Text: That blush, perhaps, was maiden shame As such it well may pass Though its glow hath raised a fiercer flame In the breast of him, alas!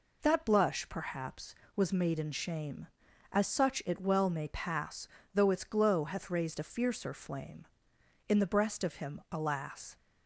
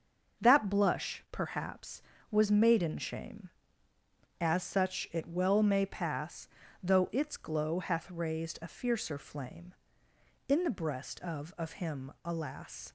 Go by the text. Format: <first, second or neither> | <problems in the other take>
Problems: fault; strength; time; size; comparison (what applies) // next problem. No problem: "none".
first | starts louder than the rest; until 1.4 s; 6.5 dB // pauses between "pass" and "Though"; slight; at 6.4 s; 0.34 s long; slight in the first // says "of" twice; at 11.5 s